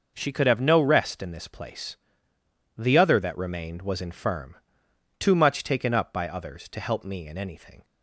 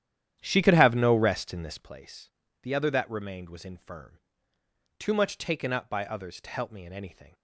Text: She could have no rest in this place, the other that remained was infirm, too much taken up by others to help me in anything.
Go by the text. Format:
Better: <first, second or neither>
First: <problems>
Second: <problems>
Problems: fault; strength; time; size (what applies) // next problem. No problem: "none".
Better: first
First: none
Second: starts louder than the rest; strong; until 1.9 s; 10.5 dB